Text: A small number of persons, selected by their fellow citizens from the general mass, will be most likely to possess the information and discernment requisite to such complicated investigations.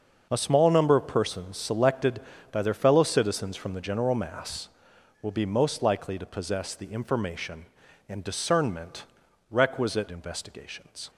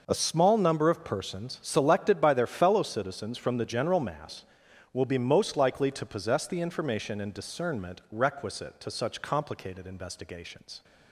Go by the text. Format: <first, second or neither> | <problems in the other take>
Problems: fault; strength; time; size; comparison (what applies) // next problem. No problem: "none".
second | starts louder than the rest; until 1.3 s; 6.5 dB // pauses between "discernment" and "requisite"; noticeable; at 9.0 s; 0.48 s long // skips "to such complicated"; at 10.0 s